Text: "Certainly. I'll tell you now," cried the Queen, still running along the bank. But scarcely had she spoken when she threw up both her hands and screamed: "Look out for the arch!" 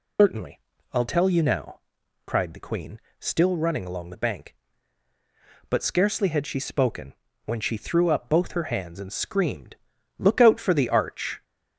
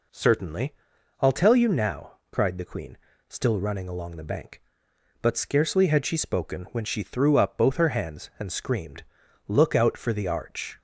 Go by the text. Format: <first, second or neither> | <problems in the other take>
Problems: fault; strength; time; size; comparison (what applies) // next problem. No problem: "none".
second | loses the start of "Certainly"; at 0.1 s; 125 ms // pauses between "spoken" and "when"; slight; at 7.1 s; 0.32 s long